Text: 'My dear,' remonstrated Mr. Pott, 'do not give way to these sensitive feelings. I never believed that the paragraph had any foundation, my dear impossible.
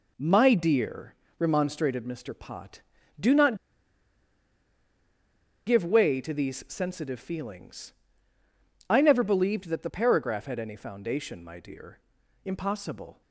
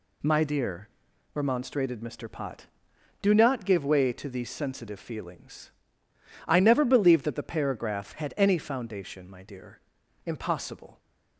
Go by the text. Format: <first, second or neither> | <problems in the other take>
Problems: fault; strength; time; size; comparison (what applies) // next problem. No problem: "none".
second | pauses between "not" and "give"; strong; at 3.5 s; 2.1 s long // pauses between "dear" and "impossible"; noticeable; at 11.9 s; 0.46 s long; noticeable in the second